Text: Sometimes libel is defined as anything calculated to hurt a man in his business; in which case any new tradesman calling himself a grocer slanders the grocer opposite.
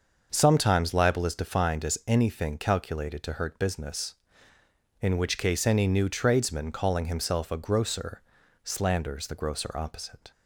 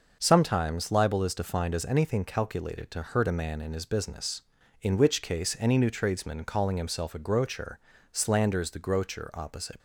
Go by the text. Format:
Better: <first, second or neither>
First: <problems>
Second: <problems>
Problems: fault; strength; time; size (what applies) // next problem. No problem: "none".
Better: second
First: starts louder than the rest; until 1.3 s; 6.5 dB // skips "a man in his"; at 3.5 s // pauses between "grocer" and "slanders"; at 8.2 s; 0.42 s long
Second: starts louder than the rest; noticeable; until 1.2 s; 6 dB // pauses between "grocer" and "slanders"; slight; at 7.7 s; 0.32 s long